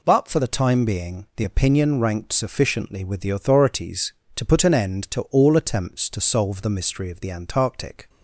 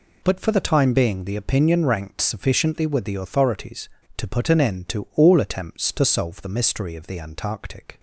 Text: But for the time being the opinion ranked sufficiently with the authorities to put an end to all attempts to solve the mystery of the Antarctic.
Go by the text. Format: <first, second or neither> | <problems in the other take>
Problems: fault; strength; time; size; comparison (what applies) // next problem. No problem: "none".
neither | none